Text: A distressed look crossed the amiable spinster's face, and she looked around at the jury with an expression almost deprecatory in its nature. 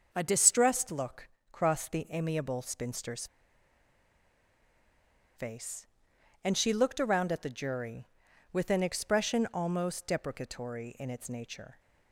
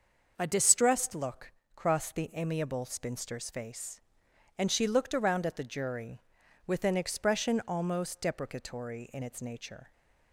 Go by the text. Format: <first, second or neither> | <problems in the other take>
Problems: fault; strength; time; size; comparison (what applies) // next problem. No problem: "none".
second | starts louder than the rest; until 1.1 s; 6.5 dB; also in the second // pauses between "look" and "crossed"; slight; at 1.2 s; 0.24 s long; slight in the second // pauses between "spinster's" and "face"; strong; at 3.2 s; 2.1 s long